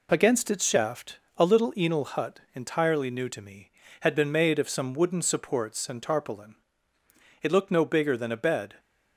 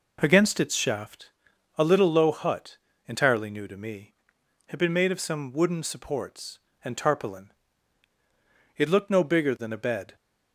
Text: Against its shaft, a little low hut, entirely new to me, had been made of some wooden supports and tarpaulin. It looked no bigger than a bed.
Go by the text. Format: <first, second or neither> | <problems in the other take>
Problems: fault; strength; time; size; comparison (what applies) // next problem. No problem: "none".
second | says "enal" for "low"; at 1.7 s